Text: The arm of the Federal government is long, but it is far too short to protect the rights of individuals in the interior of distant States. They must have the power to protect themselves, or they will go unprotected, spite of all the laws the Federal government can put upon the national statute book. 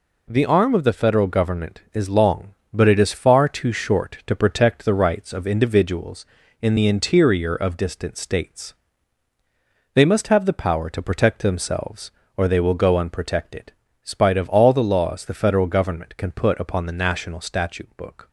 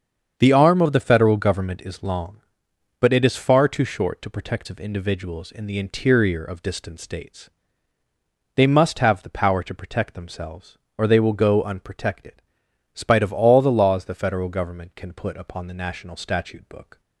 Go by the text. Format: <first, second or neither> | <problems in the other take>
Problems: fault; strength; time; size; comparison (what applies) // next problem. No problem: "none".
first | starts louder than the rest; strong; until 1.3 s; 7 dB // skips "the rights"; at 4.6 s